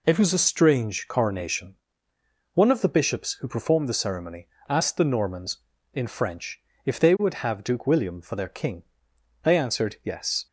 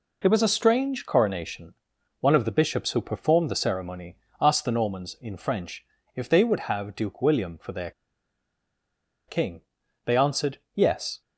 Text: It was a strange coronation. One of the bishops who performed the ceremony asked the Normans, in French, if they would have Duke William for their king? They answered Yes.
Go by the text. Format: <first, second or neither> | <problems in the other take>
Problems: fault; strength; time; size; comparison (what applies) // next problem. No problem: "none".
first | pauses between "ceremony" and "asked"; slight; at 4.1 s; 0.26 s long; slight in the first // pauses between "their" and "king"; strong; at 7.9 s; 1.3 s long // pauses between "answered" and "Yes"; slight; at 10.5 s; 0.16 s long